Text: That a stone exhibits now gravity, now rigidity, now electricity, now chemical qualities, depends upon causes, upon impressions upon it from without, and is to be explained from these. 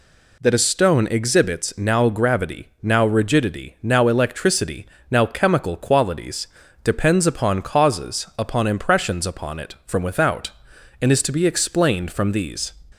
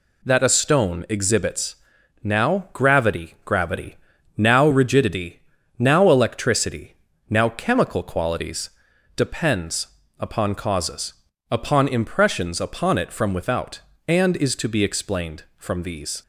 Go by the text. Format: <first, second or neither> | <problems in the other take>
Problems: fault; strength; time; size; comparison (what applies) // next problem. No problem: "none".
first | pauses between "exhibits" and "now"; noticeable; at 1.7 s; 0.48 s long // says "gravity" twice; at 3.4 s // pauses between "depends" and "upon"; slight; at 9.8 s; 0.32 s long